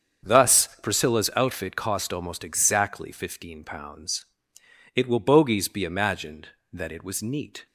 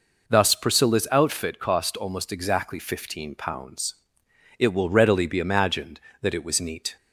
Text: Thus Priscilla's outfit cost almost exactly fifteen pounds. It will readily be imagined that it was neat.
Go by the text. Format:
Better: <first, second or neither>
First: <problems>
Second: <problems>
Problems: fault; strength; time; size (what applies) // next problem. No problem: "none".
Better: second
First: starts louder than the rest; strong; until 1.4 s; 7.5 dB // says "bogies" for "readily"; at 5.1 s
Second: none